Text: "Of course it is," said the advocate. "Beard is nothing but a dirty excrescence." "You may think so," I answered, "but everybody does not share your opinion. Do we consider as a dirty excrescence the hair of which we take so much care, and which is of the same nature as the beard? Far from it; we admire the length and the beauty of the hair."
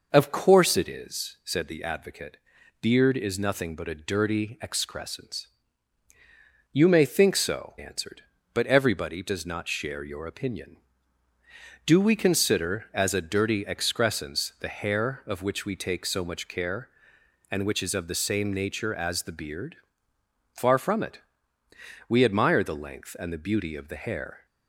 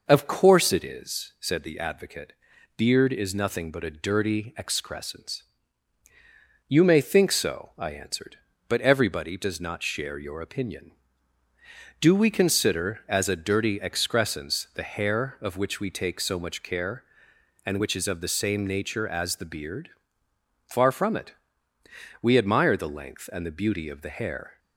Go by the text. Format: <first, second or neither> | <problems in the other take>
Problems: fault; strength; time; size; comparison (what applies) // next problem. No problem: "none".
second | skips "I"; at 7.7 s